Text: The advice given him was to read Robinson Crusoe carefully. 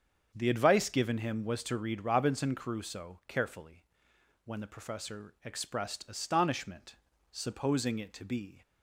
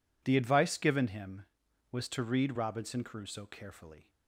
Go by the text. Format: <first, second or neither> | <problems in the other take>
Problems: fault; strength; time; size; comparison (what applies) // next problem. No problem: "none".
second | starts louder than the rest; strong; until 1.3 s; 7.5 dB // goes on to say "When the professor expressed astonishment supposing it to be"; strong; from 4.4 s on; 4.1 s long